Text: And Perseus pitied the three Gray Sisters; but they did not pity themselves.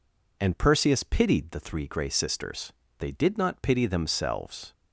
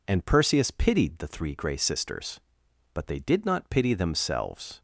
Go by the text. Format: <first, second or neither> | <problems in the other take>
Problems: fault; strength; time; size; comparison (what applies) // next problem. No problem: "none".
second | skips "but"; at 2.8 s